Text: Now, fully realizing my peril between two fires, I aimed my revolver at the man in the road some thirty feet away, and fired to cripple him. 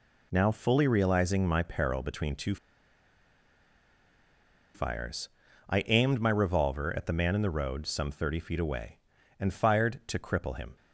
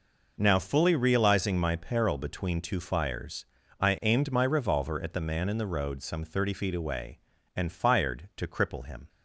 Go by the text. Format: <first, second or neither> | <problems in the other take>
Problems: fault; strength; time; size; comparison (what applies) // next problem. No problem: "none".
second | pauses between "two" and "fires"; strong; at 2.5 s; 2.1 s long